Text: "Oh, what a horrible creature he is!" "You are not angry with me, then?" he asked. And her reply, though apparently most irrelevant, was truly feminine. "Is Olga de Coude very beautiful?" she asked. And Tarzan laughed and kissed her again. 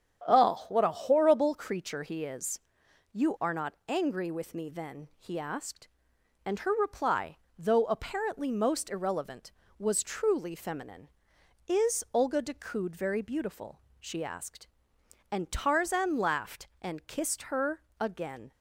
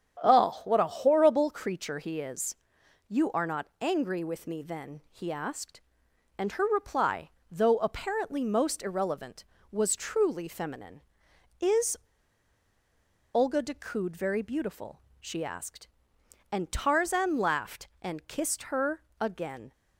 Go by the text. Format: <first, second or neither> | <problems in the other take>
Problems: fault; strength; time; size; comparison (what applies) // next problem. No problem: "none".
first | starts louder than the rest; strong; until 1.2 s; 8.5 dB; strong in the first // pauses between "Is" and "Olga"; strong; at 11.9 s; 1.3 s long // pauses between "her" and "again"; slight; at 19.0 s; 0.16 s long; slight in the first